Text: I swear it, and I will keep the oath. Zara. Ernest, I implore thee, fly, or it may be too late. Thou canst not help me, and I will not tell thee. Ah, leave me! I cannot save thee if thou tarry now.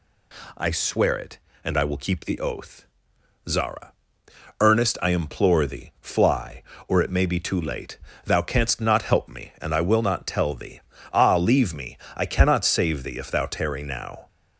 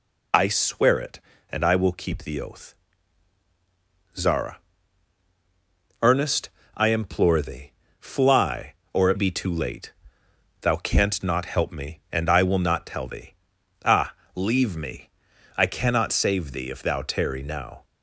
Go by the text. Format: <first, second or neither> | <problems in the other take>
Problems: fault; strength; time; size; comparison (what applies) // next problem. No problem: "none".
first | skips "may"; at 9.1 s